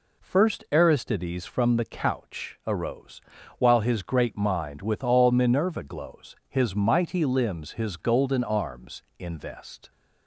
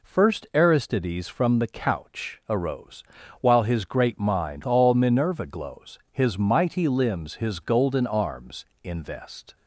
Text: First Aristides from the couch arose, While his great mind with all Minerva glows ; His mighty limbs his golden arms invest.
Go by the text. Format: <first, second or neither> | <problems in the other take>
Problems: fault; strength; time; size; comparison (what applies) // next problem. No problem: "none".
first | skips "with"; at 4.6 s // pauses between "arms" and "invest"; slight; at 8.6 s; 0.18 s long; slight in the first